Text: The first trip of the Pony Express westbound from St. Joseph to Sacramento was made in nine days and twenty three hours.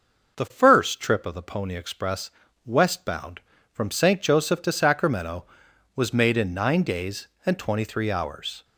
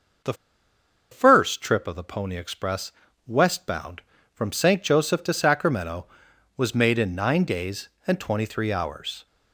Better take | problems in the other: first | starts louder than the rest; noticeable; until 2.0 s; 6 dB; noticeable in the first // pauses between "The" and "first"; noticeable; at 0.3 s; 0.78 s long // pauses between "Express" and "westbound"; slight; at 2.9 s; 0.36 s long; slight in the first

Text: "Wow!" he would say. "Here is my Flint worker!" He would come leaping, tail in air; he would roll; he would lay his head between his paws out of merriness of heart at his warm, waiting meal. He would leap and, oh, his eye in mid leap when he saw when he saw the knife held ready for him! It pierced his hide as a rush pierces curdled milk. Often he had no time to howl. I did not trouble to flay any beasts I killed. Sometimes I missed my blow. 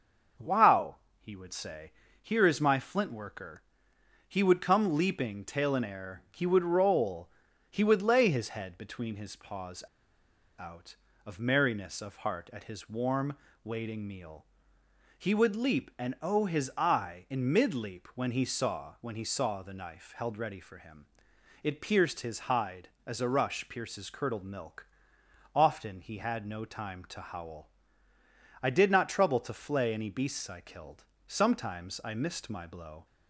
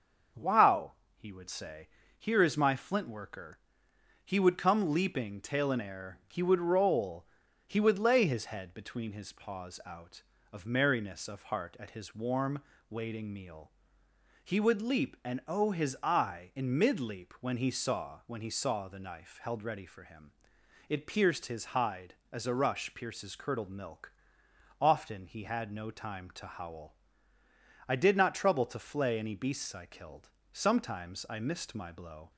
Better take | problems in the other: second | starts louder than the rest; until 1.6 s; 6 dB; also in the second // pauses between "paws" and "out"; noticeable; at 9.8 s; 0.75 s long

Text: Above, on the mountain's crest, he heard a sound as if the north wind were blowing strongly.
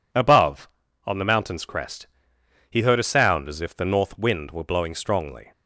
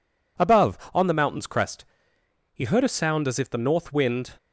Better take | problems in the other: first | stops before "were blowing strongly"; at 4.3 s

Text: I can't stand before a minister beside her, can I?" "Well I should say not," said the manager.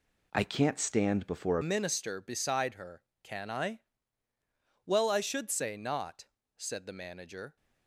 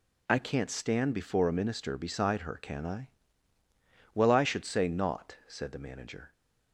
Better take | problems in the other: second | changes voice at "minister"; from 1.6 s on; 5.9 s long

